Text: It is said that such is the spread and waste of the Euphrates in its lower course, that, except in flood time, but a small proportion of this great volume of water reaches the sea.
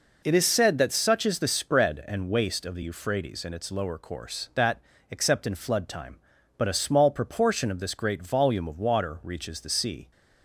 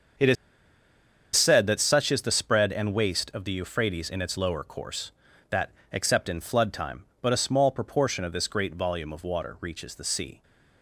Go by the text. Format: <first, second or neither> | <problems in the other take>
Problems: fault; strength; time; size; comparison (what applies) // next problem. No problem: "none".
first | starts louder than the rest; until 2.2 s; 7 dB // pauses between "is" and "said"; at 0.3 s; 1.0 s long